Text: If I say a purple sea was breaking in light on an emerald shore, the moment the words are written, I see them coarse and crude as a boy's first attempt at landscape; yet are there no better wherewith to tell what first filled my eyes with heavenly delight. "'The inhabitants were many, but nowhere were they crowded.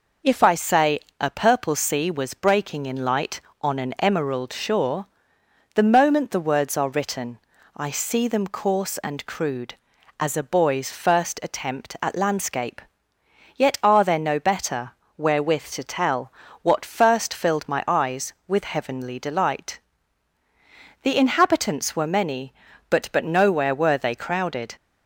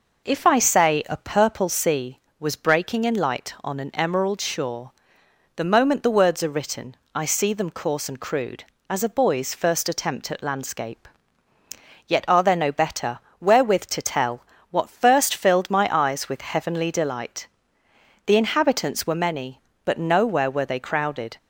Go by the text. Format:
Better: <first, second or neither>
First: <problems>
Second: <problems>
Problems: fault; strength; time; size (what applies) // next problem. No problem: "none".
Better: second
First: pauses between "say" and "a"; slight; at 0.9 s; 0.22 s long // pauses between "better" and "wherewith"; slight; at 14.9 s; 0.26 s long // pauses between "tell" and "what"; slight; at 16.3 s; 0.30 s long // says "but" twice; at 23.1 s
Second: pauses between "better" and "wherewith"; slight; at 13.1 s; 0.22 s long // pauses between "tell" and "what"; slight; at 14.4 s; 0.26 s long